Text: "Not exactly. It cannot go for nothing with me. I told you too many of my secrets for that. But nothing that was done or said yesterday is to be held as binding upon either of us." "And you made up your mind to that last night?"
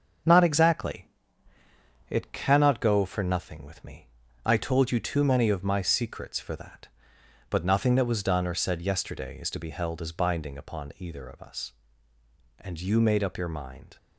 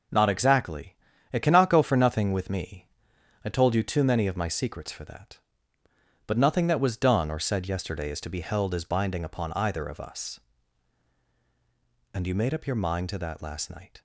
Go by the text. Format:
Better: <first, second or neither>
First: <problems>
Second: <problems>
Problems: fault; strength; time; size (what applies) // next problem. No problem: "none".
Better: second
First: starts louder than the rest; until 2.2 s; 6.5 dB // stops before "to that last night"; at 13.9 s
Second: none